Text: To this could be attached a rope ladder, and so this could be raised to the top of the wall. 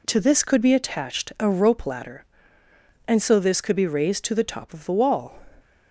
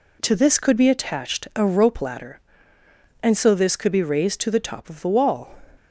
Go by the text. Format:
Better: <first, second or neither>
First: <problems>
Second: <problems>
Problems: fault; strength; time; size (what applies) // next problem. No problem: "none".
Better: neither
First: none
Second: none